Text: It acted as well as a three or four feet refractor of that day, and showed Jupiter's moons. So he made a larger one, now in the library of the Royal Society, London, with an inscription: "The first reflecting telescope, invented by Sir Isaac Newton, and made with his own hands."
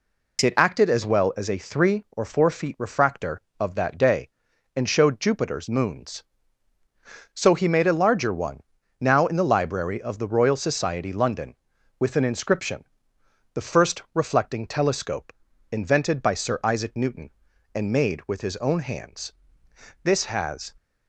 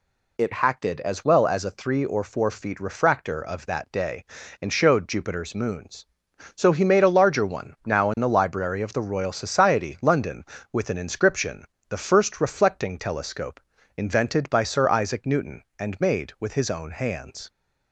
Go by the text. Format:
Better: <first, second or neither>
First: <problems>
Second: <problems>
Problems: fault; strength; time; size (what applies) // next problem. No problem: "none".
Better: second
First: goes on to say "This has"; noticeable; from 20.0 s on; 0.66 s long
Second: none